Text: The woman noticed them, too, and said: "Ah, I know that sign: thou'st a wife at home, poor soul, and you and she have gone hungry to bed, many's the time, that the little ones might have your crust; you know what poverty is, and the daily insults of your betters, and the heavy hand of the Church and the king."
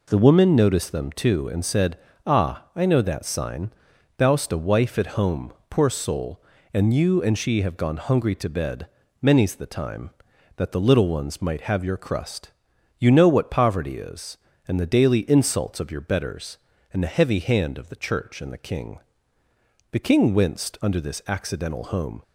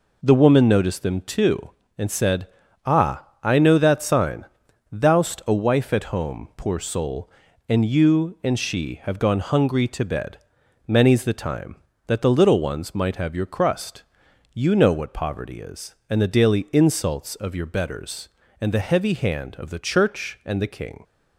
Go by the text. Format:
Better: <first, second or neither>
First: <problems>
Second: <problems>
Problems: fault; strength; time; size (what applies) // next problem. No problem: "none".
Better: second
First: goes on to say "The king winced under this accidental home"; strong; from 19.9 s on; 2.3 s long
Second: none